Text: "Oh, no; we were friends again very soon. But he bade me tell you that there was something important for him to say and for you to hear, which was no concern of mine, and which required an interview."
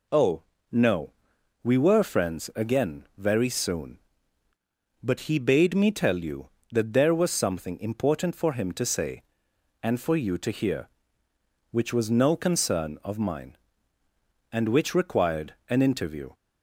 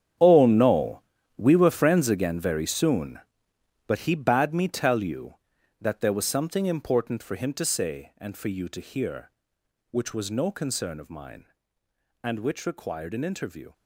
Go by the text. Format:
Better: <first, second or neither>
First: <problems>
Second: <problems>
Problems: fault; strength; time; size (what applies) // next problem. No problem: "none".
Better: first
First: none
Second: gets quieter; strong; throughout; 13.5 dB